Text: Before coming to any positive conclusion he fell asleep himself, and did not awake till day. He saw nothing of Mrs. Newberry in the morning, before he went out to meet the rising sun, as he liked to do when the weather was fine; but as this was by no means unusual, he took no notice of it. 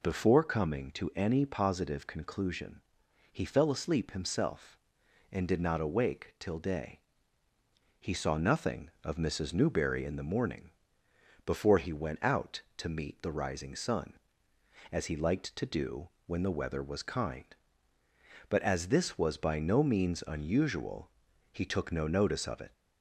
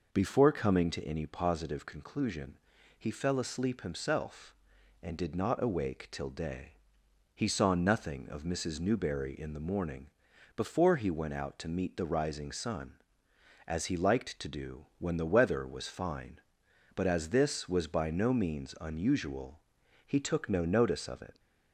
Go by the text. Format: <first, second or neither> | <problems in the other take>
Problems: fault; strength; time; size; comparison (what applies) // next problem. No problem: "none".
second | pauses between "conclusion" and "he"; noticeable; at 2.8 s; 0.54 s long; also in the second // pauses between "do" and "when"; slight; at 16.0 s; 0.18 s long // says "kind" for "fine"; at 17.0 s